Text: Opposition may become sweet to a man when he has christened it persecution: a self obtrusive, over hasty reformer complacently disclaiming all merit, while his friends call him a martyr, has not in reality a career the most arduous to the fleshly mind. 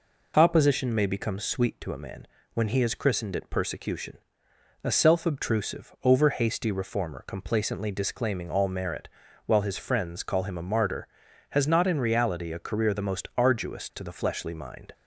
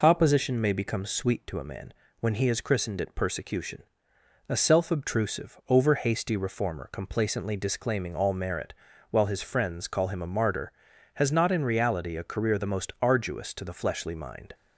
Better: neither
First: pauses between "man" and "when"; slight; at 2.2 s; 0.28 s long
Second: pauses between "man" and "when"; slight; at 1.9 s; 0.28 s long

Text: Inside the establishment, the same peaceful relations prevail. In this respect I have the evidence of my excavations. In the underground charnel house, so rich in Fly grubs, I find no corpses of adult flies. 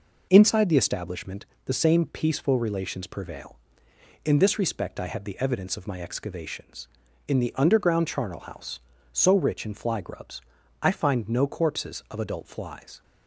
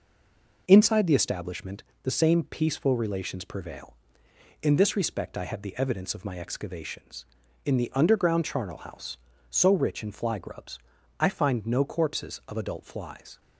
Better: first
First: none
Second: stays silent before the first word; slight; until 0.6 s; 0.6 s long

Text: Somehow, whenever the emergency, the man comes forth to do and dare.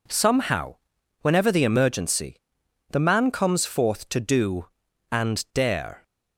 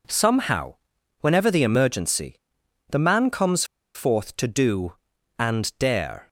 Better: first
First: none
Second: pauses between "comes" and "forth"; slight; at 3.6 s; 0.31 s long

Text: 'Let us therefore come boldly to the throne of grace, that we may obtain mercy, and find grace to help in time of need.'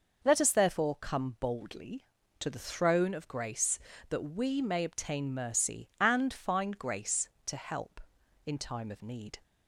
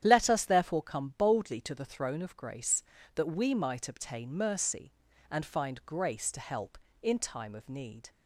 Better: first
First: none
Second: starts louder than the rest; strong; until 1.0 s; 10 dB // says "might" for "may"; at 3.5 s

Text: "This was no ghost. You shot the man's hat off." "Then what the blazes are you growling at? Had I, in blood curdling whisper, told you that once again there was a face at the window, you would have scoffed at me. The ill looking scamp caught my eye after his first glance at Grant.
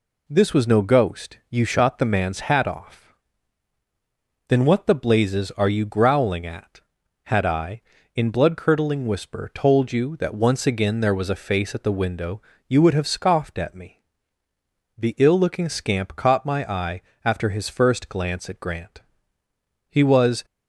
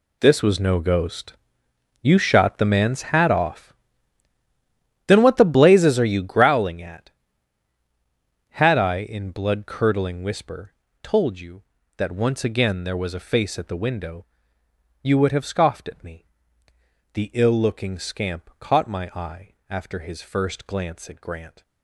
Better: second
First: pauses between "eye" and "after"; slight; at 17.0 s; 0.24 s long // goes on to say "He was"; from 19.8 s on; 0.56 s long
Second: pauses between "eye" and "after"; slight; at 19.5 s; 0.16 s long

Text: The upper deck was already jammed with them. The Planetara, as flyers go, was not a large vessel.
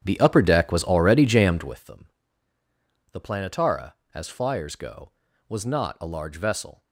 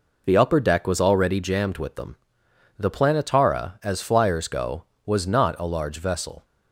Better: second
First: starts louder than the rest; strong; until 1.9 s; 9 dB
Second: none

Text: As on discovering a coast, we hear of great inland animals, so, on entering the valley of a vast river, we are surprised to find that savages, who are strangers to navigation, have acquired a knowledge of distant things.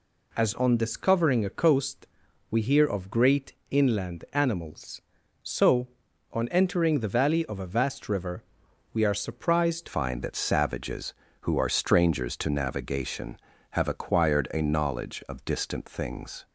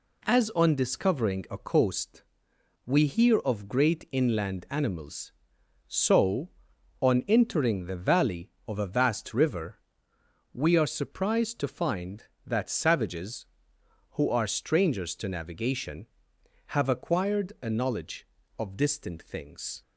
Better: second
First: pauses between "great" and "inland"; slight; at 3.5 s; 0.18 s long // changes voice at "find"; from 9.8 s on; 6.6 s long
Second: none

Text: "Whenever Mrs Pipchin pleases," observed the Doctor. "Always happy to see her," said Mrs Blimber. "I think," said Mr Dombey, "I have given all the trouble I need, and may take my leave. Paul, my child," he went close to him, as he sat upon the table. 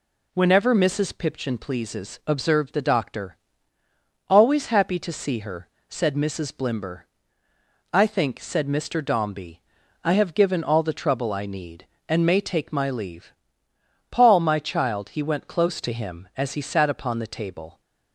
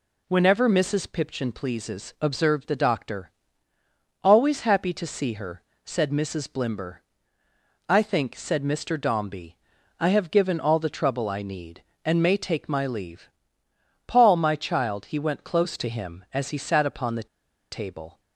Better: first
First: none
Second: pauses between "the" and "table"; at 17.2 s; 0.45 s long

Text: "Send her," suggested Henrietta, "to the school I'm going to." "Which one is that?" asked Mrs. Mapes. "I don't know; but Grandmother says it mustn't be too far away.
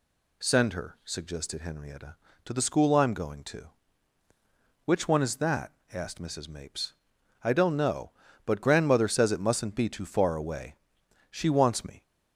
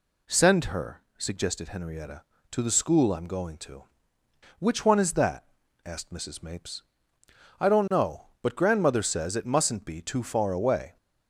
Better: second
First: goes on to say "She wants me"; noticeable; from 11.3 s on; 0.72 s long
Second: none

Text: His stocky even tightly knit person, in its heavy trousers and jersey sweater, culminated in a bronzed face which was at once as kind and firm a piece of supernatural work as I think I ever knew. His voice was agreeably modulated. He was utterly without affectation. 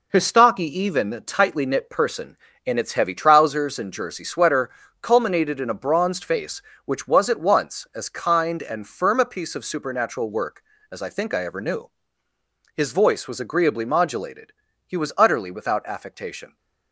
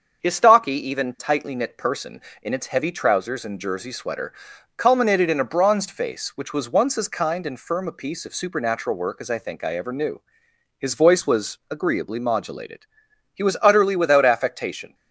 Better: first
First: none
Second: starts louder than the rest; until 1.2 s; 6.5 dB // skips "at"; at 6.6 s

